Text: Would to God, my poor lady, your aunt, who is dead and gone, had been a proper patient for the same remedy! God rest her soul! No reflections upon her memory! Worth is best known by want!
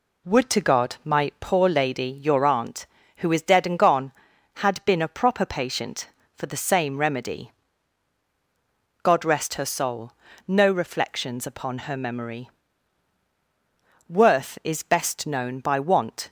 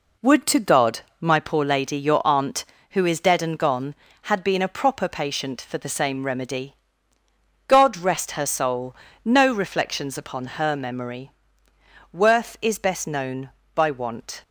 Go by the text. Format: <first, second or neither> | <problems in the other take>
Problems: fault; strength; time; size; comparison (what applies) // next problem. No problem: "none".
neither | none